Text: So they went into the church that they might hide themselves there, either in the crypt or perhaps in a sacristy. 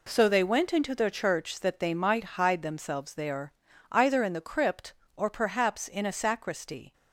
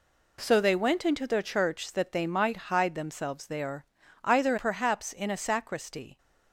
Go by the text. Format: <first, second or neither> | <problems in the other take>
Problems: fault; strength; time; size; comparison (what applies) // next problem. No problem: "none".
first | skips "in the crypt or"; at 4.5 s